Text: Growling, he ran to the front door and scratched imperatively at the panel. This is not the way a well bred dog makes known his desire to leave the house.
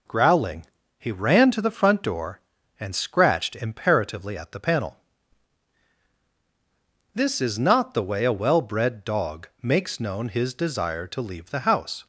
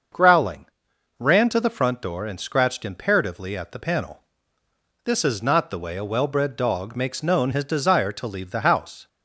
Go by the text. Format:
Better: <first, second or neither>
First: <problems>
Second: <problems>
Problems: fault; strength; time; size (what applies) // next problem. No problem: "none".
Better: first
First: none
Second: starts louder than the rest; until 1.6 s; 6.5 dB // skips "he"; at 0.9 s